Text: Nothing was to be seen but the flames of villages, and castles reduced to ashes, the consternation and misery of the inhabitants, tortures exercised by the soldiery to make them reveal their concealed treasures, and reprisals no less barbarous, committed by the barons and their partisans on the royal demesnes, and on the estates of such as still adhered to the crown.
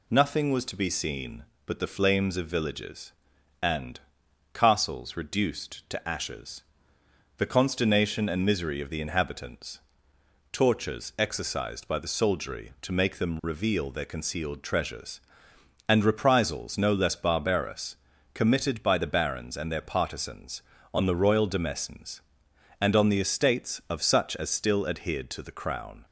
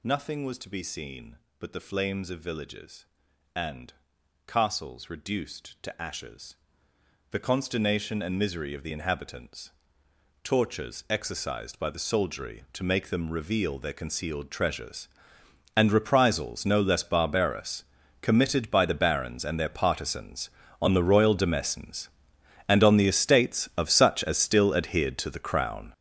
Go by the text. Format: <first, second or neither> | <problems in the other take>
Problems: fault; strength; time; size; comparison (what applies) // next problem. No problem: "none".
first | gets louder; strong; throughout; 11.5 dB // pauses between "and" and "castles"; noticeable; at 3.9 s; 0.54 s long; noticeable in the first